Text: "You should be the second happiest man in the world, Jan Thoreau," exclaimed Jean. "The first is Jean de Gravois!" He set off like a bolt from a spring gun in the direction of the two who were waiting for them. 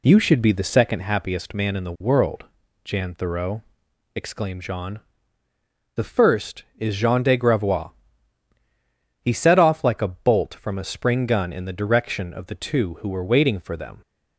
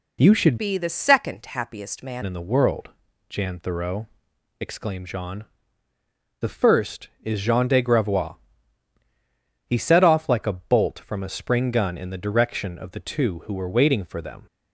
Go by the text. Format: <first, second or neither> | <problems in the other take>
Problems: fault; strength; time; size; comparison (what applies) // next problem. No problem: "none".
first | changes voice from "be" to "man"; from 0.5 to 2.2 s; 1.7 s long